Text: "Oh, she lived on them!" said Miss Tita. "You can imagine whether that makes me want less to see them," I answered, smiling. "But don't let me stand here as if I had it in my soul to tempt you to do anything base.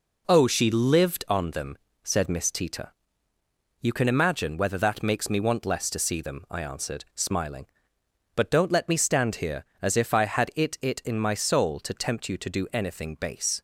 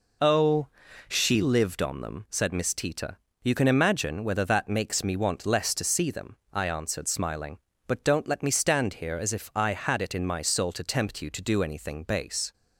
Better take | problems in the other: second | says "it" twice; at 10.8 s

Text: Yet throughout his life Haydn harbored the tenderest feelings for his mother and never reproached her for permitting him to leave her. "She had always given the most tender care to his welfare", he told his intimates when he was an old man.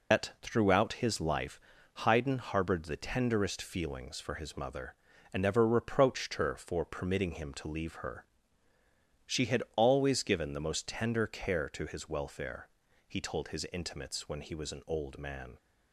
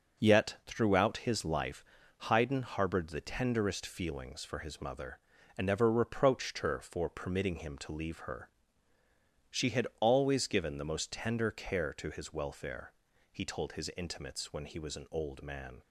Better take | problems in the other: second | loses the start of "Yet"; at 0.1 s; 155 ms // pauses between "life" and "Haydn"; noticeable; at 1.5 s; 0.46 s long; noticeable in the second

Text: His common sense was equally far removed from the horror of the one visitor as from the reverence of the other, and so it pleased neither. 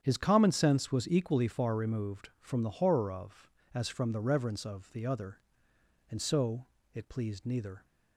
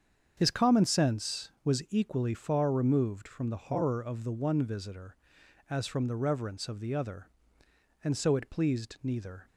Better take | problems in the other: second | starts louder than the rest; strong; until 1.0 s; 8.5 dB; strong in the second // skips "the one visitor"; at 3.6 s // pauses between "so" and "it"; slight; at 6.6 s; 0.29 s long

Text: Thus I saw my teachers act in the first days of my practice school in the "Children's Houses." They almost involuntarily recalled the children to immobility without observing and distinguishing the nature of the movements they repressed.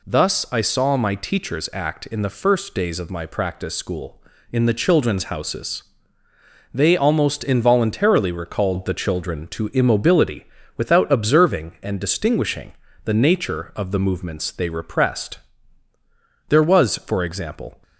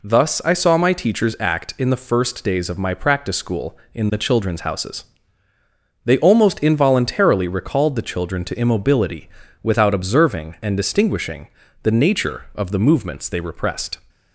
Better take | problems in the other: second | pauses between "immobility" and "without"; slight; at 10.4 s; 0.32 s long; slight in the second // pauses between "distinguishing" and "the"; slight; at 12.7 s; 0.32 s long; slight in the second // goes on to say "There was for example"; from 16.4 s on; 1.3 s long

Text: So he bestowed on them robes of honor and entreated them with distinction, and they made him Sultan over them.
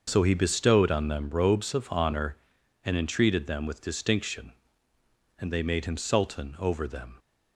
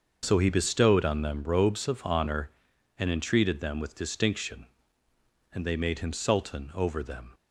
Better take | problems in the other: neither | starts louder than the rest; the same in both

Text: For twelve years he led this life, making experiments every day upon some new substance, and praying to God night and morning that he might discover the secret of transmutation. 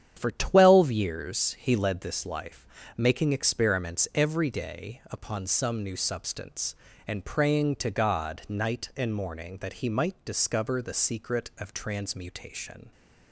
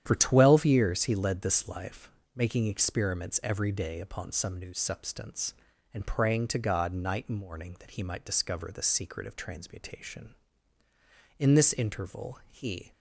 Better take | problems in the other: first | starts louder than the rest; strong; until 1.0 s; 10 dB; strong in the first // goes on to say "In this interval he"; from 11.3 s on; 1.5 s long

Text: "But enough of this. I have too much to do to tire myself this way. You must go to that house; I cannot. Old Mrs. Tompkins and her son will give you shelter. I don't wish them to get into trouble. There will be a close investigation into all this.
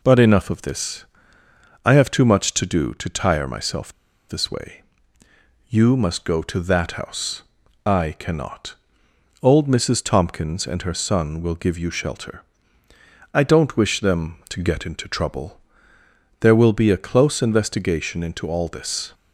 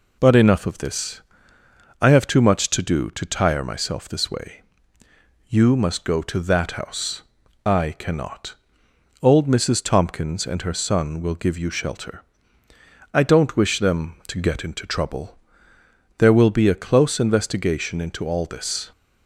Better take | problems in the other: second | pauses between "myself" and "this"; at 3.9 s; 0.37 s long

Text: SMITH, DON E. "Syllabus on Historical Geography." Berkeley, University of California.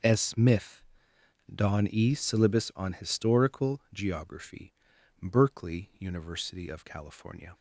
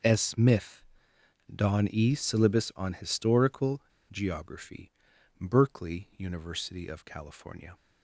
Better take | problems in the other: first | pauses between "Historical" and "Geography"; slight; at 3.8 s; 0.30 s long

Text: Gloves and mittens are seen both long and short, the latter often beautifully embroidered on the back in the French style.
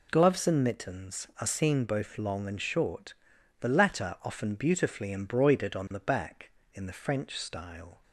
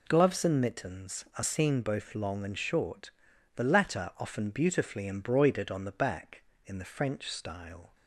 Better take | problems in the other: neither | none

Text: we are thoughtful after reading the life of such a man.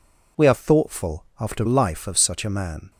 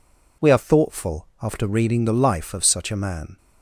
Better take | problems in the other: second | skips "reading the"; at 1.6 s

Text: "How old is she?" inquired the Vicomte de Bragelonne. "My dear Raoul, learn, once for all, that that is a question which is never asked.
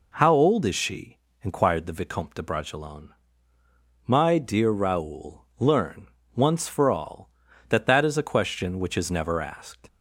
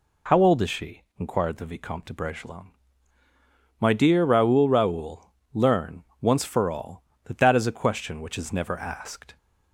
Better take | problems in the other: first | says "Raoul" twice; at 4.6 s

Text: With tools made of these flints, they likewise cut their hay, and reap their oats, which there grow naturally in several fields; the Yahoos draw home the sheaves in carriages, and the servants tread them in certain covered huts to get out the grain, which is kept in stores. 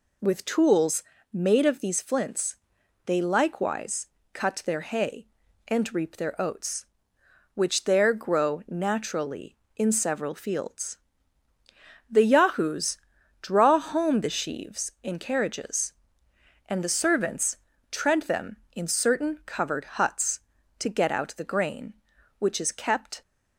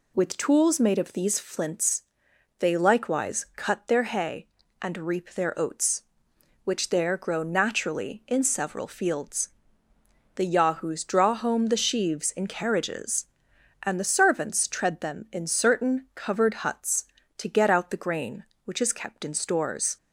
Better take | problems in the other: second | pauses between "tools" and "made"; slight; at 1.0 s; 0.30 s long // pauses between "likewise" and "cut"; slight; at 4.0 s; 0.26 s long // pauses between "Yahoos" and "draw"; at 12.9 s; 0.42 s long // pauses between "servants" and "tread"; slight; at 17.5 s; 0.36 s long // stops before "in stores"; at 23.2 s

